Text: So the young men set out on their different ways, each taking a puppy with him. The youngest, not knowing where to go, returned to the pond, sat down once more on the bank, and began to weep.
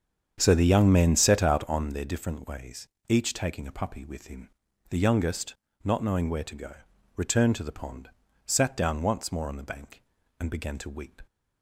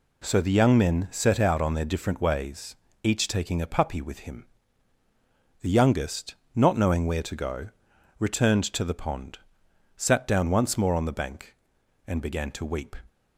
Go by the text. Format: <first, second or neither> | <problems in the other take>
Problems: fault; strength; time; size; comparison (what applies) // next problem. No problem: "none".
second | starts louder than the rest; strong; until 1.9 s; 8 dB